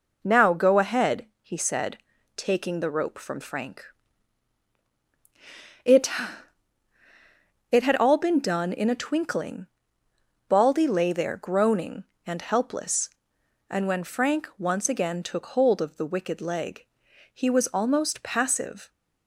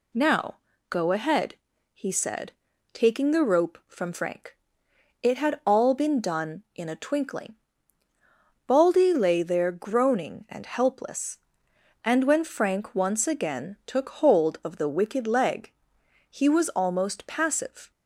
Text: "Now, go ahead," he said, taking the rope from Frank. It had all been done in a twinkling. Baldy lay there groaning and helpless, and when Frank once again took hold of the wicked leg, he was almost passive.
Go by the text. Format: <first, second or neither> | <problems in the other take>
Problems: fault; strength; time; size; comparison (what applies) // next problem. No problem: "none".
second | says "It" twice; at 7.7 s